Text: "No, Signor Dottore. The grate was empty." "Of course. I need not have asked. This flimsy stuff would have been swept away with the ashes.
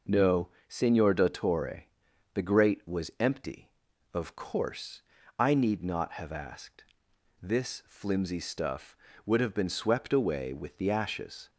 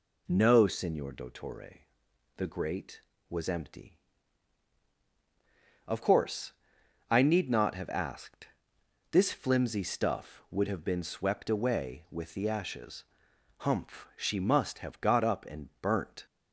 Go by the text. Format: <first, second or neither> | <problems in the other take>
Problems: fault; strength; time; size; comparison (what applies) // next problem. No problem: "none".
first | goes on to say "Humph She must have got up and burnt"; strong; from 13.5 s on; 2.6 s long